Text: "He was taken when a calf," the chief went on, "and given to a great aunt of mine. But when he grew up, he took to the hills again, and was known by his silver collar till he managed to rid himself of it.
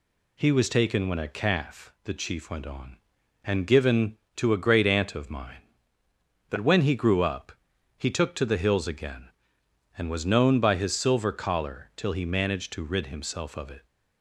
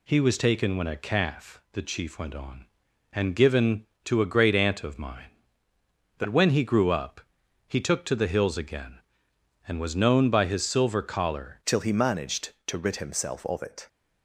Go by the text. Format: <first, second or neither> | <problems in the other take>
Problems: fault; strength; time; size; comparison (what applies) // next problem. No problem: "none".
first | changes voice at "till"; from 11.6 s on; 2.2 s long